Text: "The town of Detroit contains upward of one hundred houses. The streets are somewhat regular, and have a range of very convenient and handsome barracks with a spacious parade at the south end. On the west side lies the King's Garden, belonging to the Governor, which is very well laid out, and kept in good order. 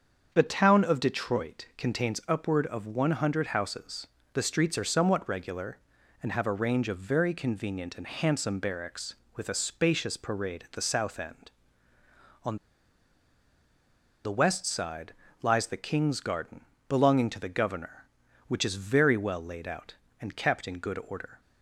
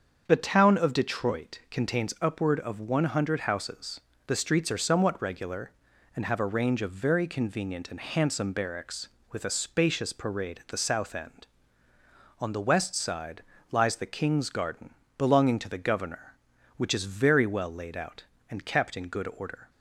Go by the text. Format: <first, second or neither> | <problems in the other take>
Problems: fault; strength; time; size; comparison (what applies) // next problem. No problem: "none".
second | starts louder than the rest; until 1.3 s; 7 dB; also in the second // pauses between "On" and "the"; strong; at 12.5 s; 1.6 s long // pauses between "side" and "lies"; slight; at 15.1 s; 0.30 s long; slight in the second